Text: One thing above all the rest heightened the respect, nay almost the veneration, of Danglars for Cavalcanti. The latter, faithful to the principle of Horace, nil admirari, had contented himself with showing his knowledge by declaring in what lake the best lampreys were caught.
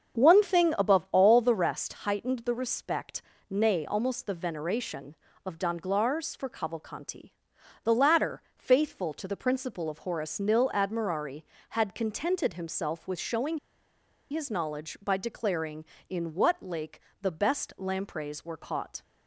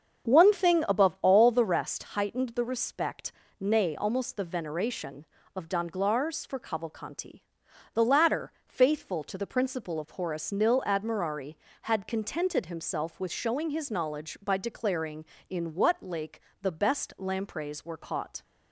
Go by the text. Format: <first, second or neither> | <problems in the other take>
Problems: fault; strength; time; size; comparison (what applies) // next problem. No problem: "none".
second | starts louder than the rest; strong; until 1.2 s; 7.5 dB; strong in the second // pauses between "showing" and "his"; noticeable; at 13.5 s; 0.72 s long // pauses between "lake" and "the"; slight; at 17.0 s; 0.20 s long; slight in the second